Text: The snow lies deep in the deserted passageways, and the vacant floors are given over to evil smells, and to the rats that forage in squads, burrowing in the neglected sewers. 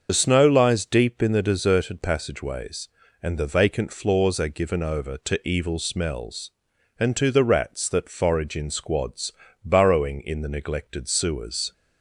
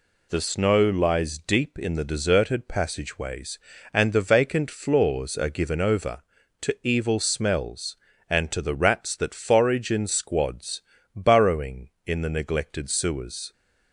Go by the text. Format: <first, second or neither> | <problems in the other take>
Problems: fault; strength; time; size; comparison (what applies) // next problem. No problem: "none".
second | loses the start of "The"; at 0.0 s; 30 ms // starts louder than the rest; until 1.1 s; 6.5 dB